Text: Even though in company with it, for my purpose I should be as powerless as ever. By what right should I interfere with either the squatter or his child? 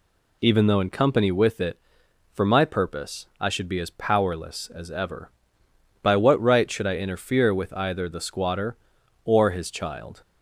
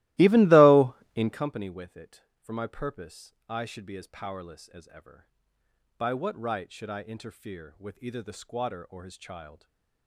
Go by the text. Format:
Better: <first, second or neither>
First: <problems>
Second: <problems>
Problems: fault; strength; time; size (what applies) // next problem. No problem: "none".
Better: first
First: pauses between "purpose" and "I"; slight; at 3.2 s; 0.16 s long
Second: starts louder than the rest; strong; until 1.5 s; 17.5 dB // pauses between "purpose" and "I"; slight; at 3.3 s; 0.16 s long // stays silent after the last word; slight; from 9.5 s on; 0.5 s long